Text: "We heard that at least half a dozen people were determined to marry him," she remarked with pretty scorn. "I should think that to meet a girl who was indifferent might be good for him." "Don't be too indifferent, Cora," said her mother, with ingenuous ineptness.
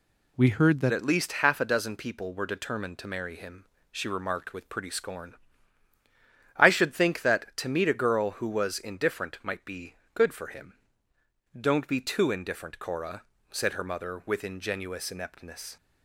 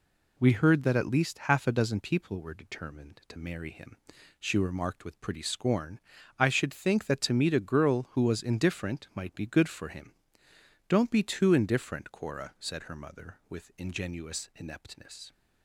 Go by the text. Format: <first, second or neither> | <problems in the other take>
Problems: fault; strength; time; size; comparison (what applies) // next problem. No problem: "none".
second | changes voice at "at"; from 0.9 s on; 14.8 s long // pauses between "be" and "good"; slight; at 9.9 s; 0.18 s long